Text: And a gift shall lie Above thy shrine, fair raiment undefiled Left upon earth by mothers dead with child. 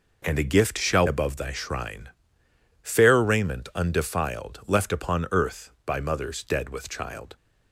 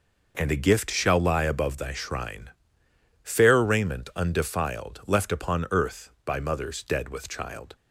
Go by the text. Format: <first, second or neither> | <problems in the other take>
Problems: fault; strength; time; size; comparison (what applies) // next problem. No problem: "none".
second | skips "lie"; at 1.0 s